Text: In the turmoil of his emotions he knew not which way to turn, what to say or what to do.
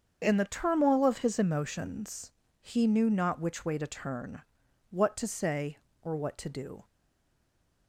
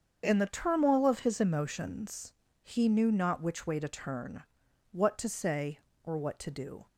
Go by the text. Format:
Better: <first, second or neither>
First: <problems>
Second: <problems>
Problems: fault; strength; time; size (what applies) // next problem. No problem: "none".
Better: second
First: starts louder than the rest; strong; until 1.2 s; 7 dB // pauses between "emotions" and "he"; slight; at 2.3 s; 0.30 s long // stays silent after the last word; from 6.8 s on; 1.0 s long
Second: starts louder than the rest; strong; until 1.2 s; 7 dB // pauses between "emotions" and "he"; slight; at 2.3 s; 0.30 s long